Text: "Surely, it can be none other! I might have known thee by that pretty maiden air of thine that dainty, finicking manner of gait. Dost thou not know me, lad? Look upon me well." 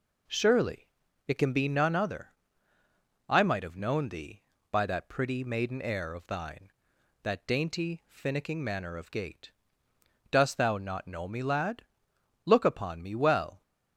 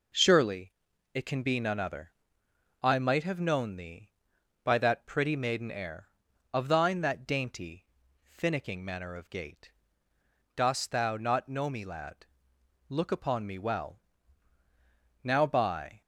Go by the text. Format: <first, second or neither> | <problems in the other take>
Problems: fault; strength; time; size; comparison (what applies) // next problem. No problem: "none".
first | goes on to say "Now by"; noticeable; from 15.2 s on; 0.78 s long